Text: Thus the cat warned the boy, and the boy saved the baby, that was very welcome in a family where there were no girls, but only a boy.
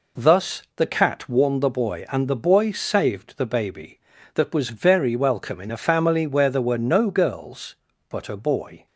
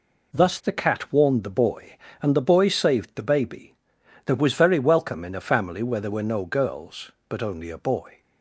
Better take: second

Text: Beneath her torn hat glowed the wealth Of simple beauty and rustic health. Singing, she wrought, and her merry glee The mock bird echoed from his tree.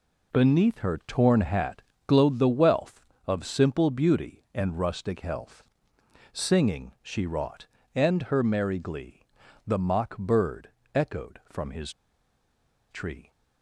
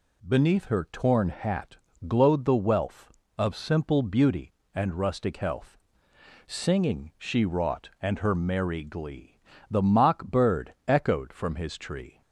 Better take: second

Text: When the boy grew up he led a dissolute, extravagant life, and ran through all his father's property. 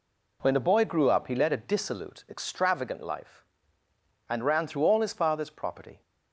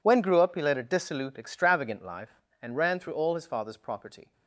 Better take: first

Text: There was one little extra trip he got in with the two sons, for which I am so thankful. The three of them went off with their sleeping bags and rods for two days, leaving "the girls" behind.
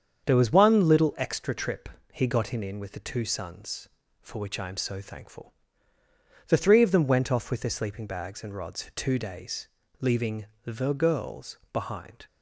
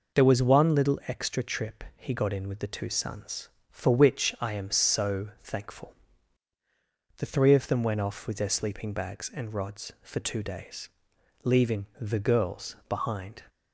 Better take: second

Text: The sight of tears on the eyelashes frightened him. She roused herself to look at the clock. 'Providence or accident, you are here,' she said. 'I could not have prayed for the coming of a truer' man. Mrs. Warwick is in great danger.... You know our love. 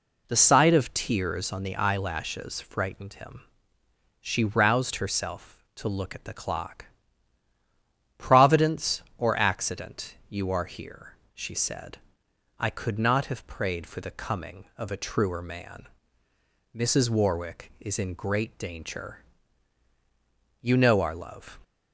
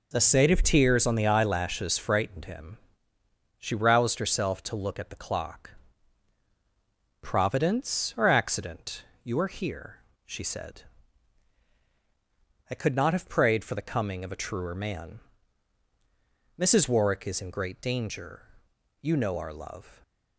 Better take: neither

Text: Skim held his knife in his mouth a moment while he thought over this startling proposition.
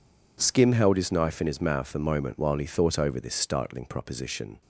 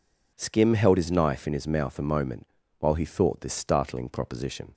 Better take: first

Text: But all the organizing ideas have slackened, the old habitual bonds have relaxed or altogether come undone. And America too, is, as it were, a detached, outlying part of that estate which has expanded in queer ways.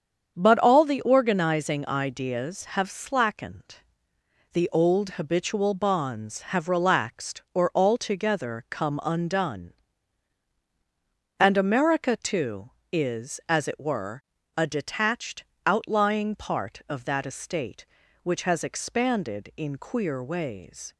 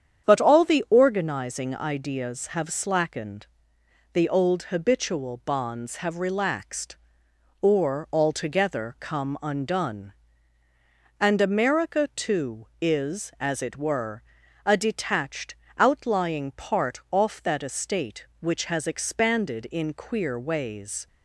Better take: first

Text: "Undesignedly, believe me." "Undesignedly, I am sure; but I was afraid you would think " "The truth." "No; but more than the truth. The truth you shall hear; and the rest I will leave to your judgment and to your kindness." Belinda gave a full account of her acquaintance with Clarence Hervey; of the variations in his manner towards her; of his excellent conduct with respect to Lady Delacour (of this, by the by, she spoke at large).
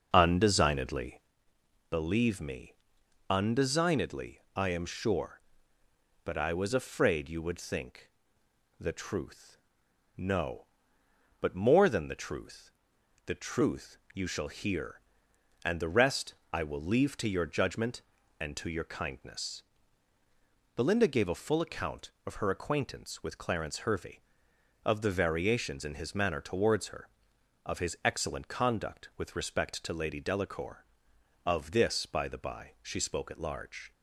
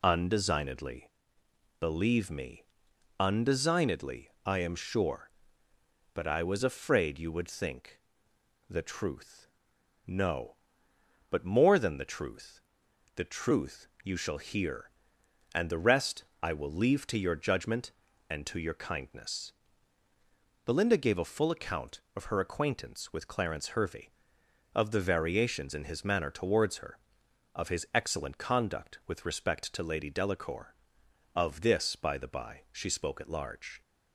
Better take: second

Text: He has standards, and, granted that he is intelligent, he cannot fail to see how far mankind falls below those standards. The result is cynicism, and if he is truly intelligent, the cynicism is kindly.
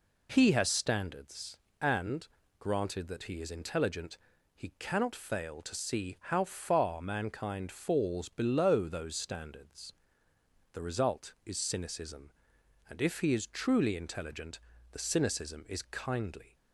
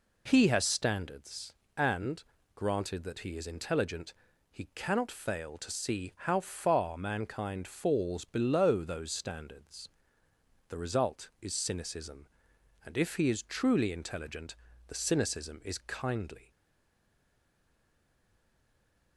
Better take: first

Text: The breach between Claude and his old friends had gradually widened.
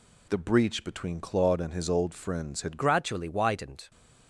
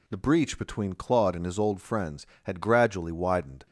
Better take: second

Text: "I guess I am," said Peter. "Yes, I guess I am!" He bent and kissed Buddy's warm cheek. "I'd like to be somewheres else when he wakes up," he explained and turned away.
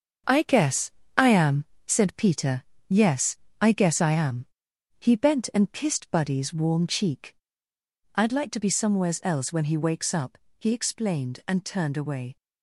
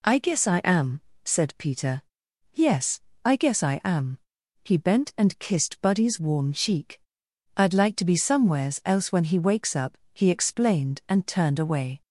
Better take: second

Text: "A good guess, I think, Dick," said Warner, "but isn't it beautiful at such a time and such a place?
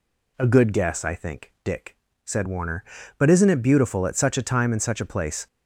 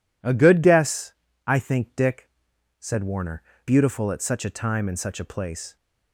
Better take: first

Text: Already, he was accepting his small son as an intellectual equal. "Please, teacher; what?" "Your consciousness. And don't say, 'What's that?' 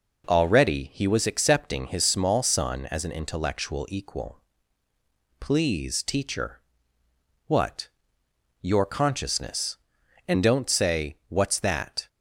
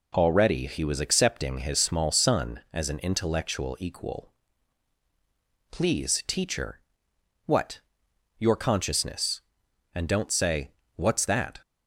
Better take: neither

